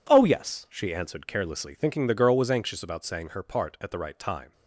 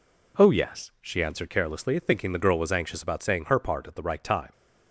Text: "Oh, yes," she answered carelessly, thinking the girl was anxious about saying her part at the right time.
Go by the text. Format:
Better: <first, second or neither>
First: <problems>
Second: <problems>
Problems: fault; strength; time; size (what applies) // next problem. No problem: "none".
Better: neither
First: none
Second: none